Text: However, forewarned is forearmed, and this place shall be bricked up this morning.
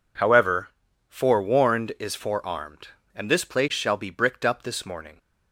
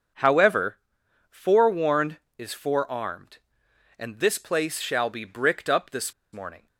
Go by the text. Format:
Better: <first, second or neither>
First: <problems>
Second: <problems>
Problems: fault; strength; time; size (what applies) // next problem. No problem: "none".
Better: first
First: none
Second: starts louder than the rest; until 1.6 s; 6.5 dB // pauses between "this" and "morning"; slight; at 6.1 s; 0.19 s long